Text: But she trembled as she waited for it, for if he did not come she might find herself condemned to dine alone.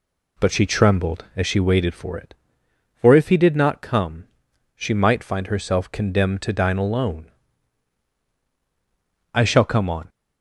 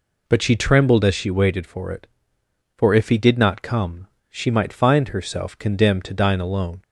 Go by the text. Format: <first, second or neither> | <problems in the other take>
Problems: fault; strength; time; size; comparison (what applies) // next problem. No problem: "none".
second | pauses between "come" and "she"; noticeable; at 4.2 s; 0.54 s long; slight in the second // goes on to say "I shall come on"; noticeable; from 9.3 s on; 0.76 s long